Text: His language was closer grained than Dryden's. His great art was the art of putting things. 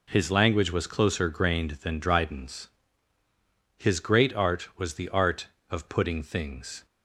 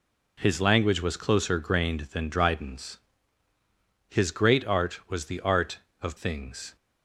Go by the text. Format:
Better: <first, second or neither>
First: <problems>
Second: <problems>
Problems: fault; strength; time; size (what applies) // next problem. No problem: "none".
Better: first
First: none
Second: skips "putting"; at 6.1 s